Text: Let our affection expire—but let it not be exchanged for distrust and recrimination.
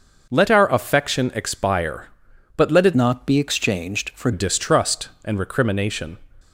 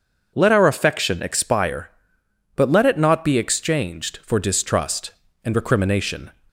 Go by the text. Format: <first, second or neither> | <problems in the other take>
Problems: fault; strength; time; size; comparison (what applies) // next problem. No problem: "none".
second | changes voice from "not" to "for"; from 2.9 to 4.3 s; 1.4 s long